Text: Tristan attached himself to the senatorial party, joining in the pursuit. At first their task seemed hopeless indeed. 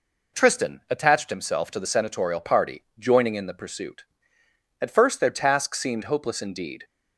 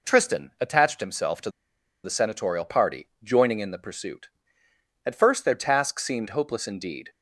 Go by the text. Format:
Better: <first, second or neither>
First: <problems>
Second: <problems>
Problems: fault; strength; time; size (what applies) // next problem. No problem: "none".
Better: first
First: none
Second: pauses between "to" and "the"; noticeable; at 1.4 s; 0.55 s long